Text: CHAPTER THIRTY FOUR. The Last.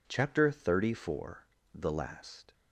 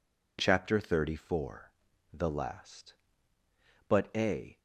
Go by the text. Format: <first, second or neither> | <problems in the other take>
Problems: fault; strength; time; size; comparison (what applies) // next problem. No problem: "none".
first | goes on to say "But a"; noticeable; from 3.8 s on; 0.68 s long